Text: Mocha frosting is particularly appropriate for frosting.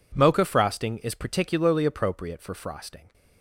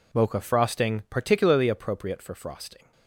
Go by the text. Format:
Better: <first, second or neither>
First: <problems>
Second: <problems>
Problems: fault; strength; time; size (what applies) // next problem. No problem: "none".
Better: first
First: none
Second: skips "is"; at 1.0 s